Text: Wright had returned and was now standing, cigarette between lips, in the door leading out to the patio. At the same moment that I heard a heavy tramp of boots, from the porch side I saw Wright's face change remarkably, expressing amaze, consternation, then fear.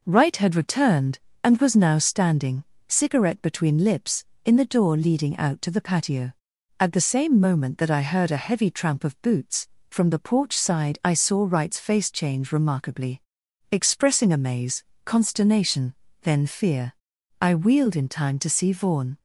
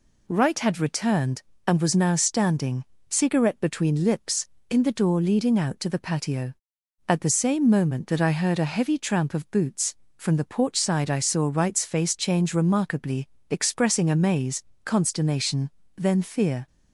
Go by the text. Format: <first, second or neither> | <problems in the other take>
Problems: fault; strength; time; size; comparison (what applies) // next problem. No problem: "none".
second | goes on to say "I wheeled in time to see Vaughn"; strong; from 17.4 s on; 1.7 s long